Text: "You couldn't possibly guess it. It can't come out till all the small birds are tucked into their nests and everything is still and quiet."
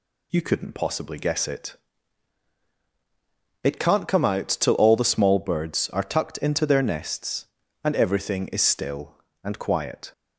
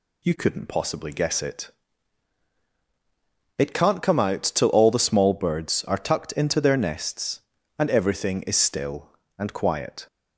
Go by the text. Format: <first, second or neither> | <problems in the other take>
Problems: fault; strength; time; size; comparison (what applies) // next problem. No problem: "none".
neither | none